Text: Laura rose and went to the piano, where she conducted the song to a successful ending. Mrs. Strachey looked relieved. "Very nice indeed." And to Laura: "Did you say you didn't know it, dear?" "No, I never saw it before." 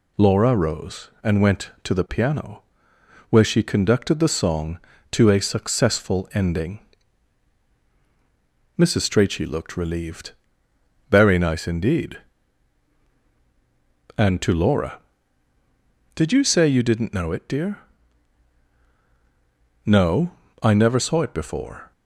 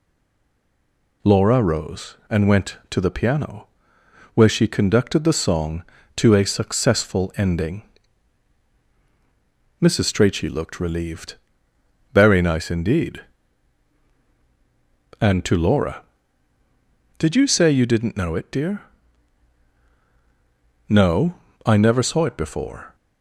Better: first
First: none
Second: stays silent before the first word; noticeable; until 1.2 s; 1.2 s long

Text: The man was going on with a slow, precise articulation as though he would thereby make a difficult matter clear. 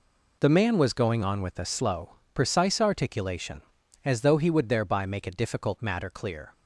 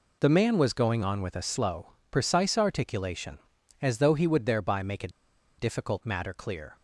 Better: first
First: none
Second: pauses between "a" and "difficult"; noticeable; at 5.0 s; 0.49 s long

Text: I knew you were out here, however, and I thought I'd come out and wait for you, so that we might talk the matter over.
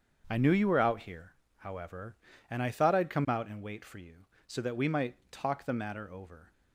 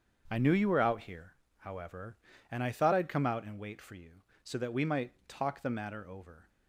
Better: neither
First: starts louder than the rest; until 1.3 s; 7 dB // pauses between "might" and "talk"; slight; at 5.1 s; 0.16 s long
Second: starts louder than the rest; until 1.3 s; 7 dB // pauses between "might" and "talk"; slight; at 5.1 s; 0.16 s long

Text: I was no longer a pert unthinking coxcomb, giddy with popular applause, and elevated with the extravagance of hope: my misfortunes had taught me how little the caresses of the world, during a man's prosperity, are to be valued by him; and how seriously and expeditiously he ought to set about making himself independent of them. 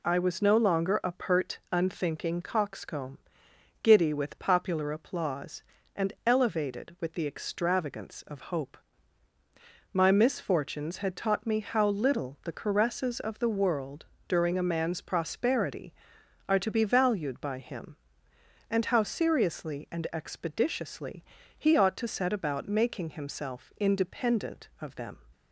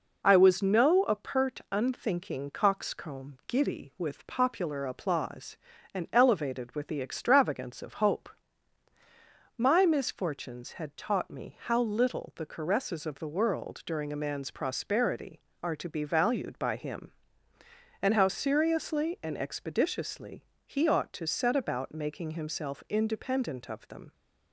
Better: first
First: pauses between "expeditiously" and "he"; slight; at 21.2 s; 0.32 s long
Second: skips "longer"; at 1.0 s // pauses between "expeditiously" and "he"; slight; at 20.4 s; 0.22 s long

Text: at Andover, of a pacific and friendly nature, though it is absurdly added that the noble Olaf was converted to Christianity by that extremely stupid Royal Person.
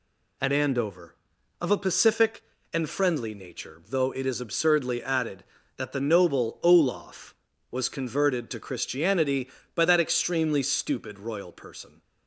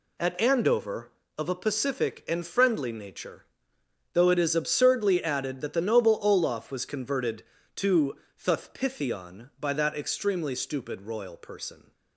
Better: first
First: none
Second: says "Thuthpithion" for "Christianity"; at 8.4 s

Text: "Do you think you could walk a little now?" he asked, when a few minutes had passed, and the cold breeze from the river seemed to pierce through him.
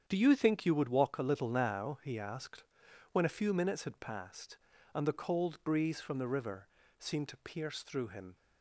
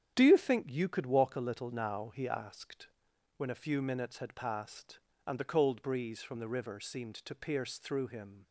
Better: second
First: starts louder than the rest; strong; until 1.0 s; 8.5 dB // says "would" for "could"; at 0.7 s // pauses between "river" and "seemed"; slight; at 6.6 s; 0.30 s long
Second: starts louder than the rest; strong; until 1.1 s; 9 dB

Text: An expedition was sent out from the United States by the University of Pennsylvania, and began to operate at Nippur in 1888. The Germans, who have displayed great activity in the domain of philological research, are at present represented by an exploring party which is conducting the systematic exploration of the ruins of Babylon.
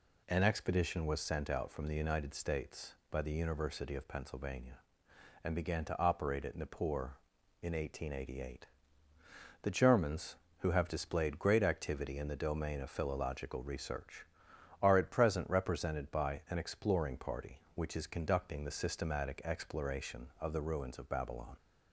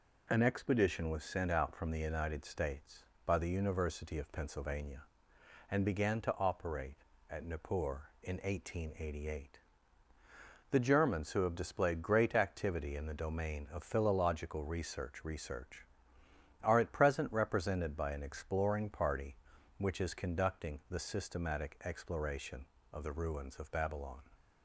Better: first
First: none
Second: says "research" twice; at 15.2 s

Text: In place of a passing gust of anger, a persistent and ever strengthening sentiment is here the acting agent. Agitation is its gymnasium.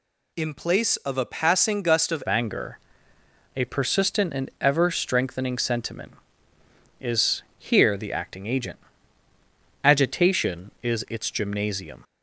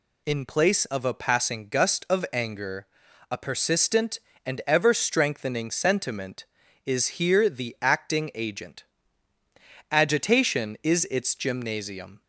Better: second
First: changes voice at "anger"; from 2.2 s on; 9.8 s long // pauses between "is" and "here"; slight; at 7.4 s; 0.16 s long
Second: none

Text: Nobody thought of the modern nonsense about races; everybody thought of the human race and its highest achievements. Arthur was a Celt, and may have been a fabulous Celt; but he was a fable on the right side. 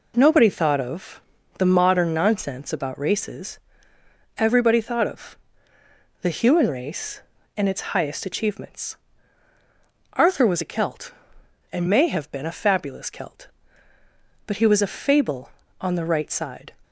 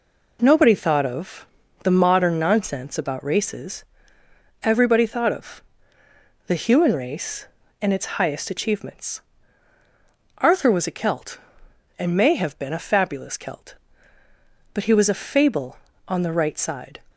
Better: neither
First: pauses between "of" and "the"; slight; at 1.2 s; 0.36 s long // pauses between "of" and "the"; noticeable; at 5.3 s; 0.84 s long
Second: pauses between "of" and "the"; slight; at 1.4 s; 0.36 s long // pauses between "of" and "the"; noticeable; at 5.6 s; 0.84 s long

